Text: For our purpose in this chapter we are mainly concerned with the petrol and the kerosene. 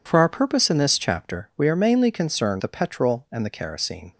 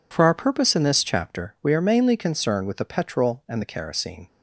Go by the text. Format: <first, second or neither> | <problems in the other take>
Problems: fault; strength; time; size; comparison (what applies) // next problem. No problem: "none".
second | skips "with"; at 2.5 s